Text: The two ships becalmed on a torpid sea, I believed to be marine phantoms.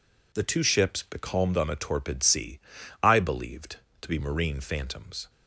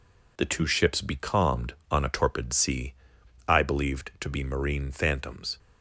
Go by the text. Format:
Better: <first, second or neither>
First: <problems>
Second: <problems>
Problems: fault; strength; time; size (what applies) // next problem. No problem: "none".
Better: neither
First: none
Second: none